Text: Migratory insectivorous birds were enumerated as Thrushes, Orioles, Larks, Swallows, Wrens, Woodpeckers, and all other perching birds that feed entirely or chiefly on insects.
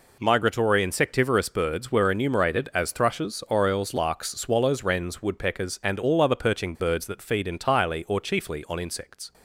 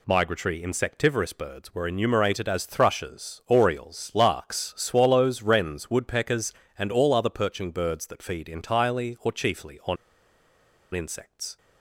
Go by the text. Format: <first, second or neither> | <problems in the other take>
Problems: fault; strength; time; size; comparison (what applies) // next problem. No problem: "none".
first | pauses between "on" and "insects"; at 9.9 s; 0.98 s long